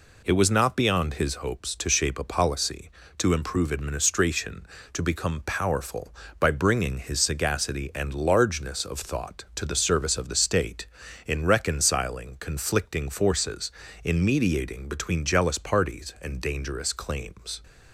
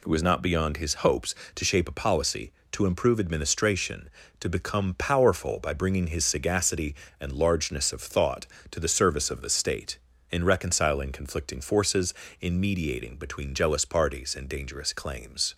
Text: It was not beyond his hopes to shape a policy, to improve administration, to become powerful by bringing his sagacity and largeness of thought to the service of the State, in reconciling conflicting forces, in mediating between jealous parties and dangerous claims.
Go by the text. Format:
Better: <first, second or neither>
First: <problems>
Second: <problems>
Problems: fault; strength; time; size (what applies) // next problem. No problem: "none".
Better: neither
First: none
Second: none